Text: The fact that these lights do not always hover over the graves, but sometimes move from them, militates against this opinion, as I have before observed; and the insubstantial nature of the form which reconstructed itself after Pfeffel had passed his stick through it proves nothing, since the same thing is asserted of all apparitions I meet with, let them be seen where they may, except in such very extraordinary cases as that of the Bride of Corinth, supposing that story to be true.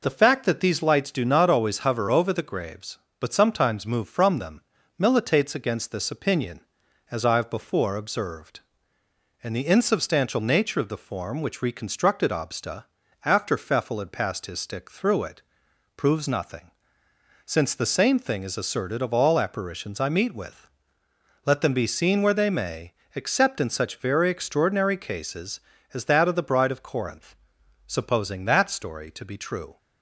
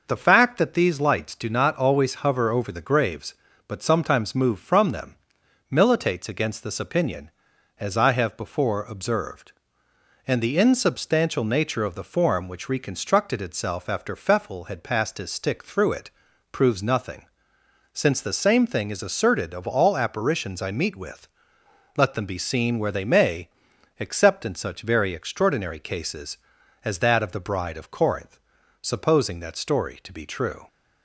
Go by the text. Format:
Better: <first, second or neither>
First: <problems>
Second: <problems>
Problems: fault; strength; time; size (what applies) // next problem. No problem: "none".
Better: second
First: says "obsta" for "itself"; at 12.3 s // pauses between "it" and "proves"; noticeable; at 15.4 s; 0.54 s long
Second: pauses between "it" and "proves"; at 16.0 s; 0.44 s long